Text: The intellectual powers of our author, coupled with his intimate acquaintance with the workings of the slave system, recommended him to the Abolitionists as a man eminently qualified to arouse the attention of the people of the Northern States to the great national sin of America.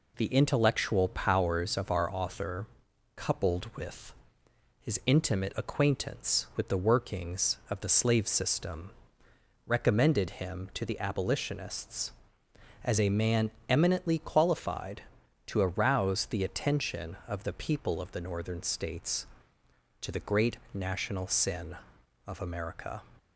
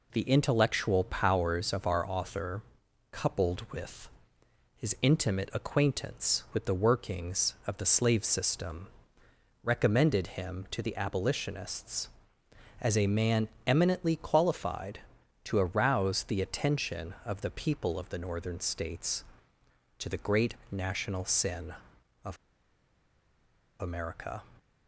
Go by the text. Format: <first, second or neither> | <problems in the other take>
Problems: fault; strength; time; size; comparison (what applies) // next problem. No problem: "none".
first | pauses between "with" and "his"; noticeable; at 4.0 s; 0.66 s long; noticeable in the first // pauses between "man" and "eminently"; slight; at 13.4 s; 0.18 s long; slight in the first // pauses between "great" and "national"; slight; at 20.5 s; 0.16 s long; slight in the first // pauses between "of" and "America"; strong; at 22.3 s; 1.4 s long